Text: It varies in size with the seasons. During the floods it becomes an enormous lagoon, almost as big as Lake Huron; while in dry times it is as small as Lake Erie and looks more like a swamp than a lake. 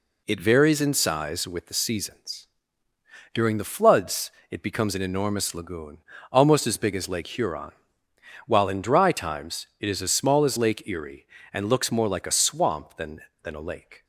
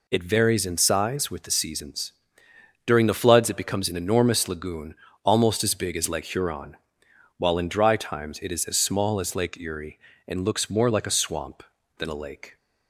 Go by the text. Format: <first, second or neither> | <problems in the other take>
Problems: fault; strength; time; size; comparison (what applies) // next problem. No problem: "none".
second | pauses between "floods" and "it"; slight; at 4.3 s; 0.18 s long // pauses between "times" and "it"; slight; at 9.6 s; 0.16 s long // says "than" twice; at 13.4 s